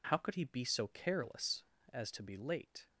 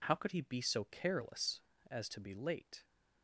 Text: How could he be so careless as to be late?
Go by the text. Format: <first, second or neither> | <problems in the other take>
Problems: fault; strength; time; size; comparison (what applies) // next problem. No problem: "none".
neither | none